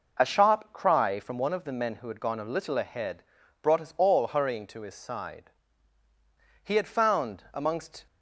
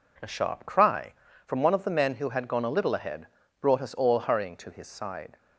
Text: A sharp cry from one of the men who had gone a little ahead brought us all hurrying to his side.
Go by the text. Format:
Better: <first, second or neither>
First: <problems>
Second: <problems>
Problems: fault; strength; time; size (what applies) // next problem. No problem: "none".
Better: second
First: pauses between "ahead" and "brought"; at 3.2 s; 0.40 s long // goes on to say "He had found amongst"; from 6.6 s on; 1.4 s long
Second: pauses between "ahead" and "brought"; slight; at 3.2 s; 0.32 s long